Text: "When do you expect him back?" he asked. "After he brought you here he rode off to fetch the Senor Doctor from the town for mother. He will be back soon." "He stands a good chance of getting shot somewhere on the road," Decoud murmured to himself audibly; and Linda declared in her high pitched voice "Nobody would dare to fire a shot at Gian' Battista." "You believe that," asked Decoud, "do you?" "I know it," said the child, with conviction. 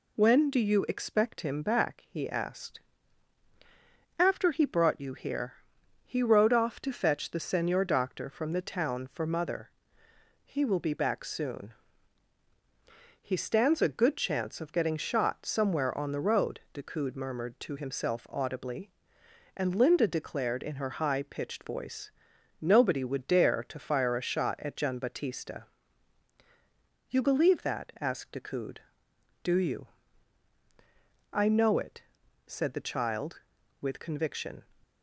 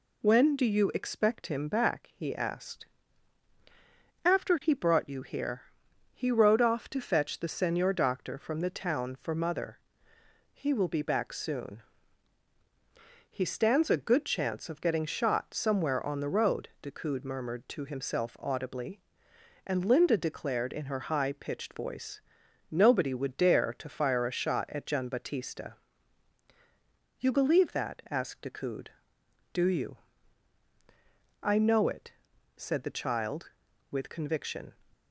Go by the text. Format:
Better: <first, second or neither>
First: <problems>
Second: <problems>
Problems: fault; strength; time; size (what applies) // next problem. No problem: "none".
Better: neither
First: pauses between "here" and "he"; noticeable; at 5.5 s; 0.50 s long // pauses between "voice" and "Nobody"; noticeable; at 22.1 s; 0.50 s long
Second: pauses between "here" and "he"; noticeable; at 5.6 s; 0.50 s long // pauses between "voice" and "Nobody"; noticeable; at 22.2 s; 0.50 s long